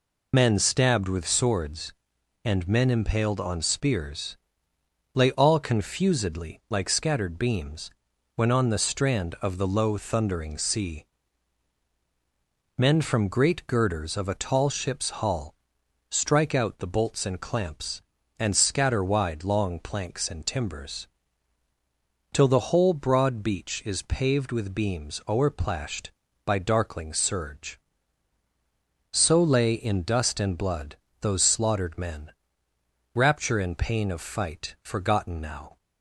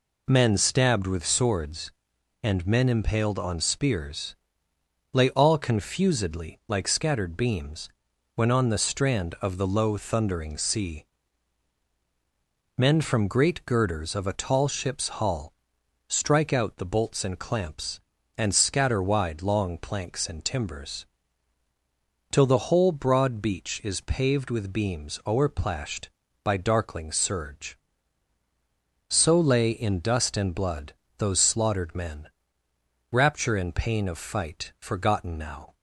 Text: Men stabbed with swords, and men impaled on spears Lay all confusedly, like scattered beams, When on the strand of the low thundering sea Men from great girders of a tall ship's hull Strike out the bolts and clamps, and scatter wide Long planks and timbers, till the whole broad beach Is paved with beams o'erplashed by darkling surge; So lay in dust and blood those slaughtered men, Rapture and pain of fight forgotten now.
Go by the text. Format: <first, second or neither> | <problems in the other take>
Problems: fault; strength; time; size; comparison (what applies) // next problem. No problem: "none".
second | loses the start of "Men"; at 0.3 s; 40 ms // pauses between "spears" and "Lay"; noticeable; at 4.3 s; 0.78 s long; noticeable in the second // pauses between "sea" and "Men"; strong; at 11.0 s; 1.7 s long; strong in the second // pauses between "hull" and "Strike"; noticeable; at 15.5 s; 0.56 s long; noticeable in the second // pauses between "blood" and "those"; slight; at 30.9 s; 0.26 s long; slight in the second